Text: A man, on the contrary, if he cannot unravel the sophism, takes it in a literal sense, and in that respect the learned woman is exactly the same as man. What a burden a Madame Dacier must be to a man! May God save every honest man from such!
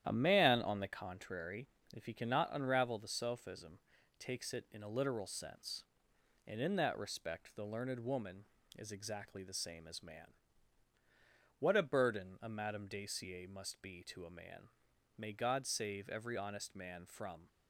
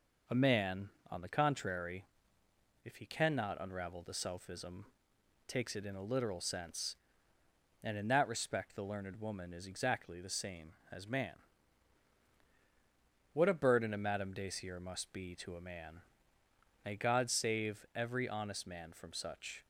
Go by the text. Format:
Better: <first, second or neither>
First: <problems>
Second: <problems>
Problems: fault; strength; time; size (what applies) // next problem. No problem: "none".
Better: second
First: starts louder than the rest; strong; until 1.0 s; 10.5 dB // stops before "such"; at 17.4 s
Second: none